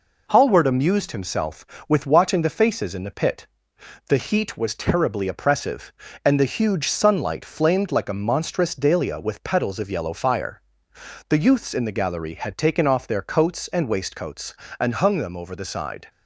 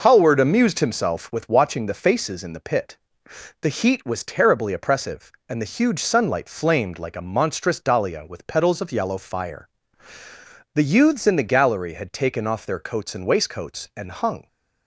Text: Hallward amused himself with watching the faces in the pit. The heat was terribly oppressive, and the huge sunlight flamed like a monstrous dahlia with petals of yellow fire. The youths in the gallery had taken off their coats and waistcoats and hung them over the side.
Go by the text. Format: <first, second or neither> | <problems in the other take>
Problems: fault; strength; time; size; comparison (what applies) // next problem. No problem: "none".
first | stops before "them over the side"; at 14.4 s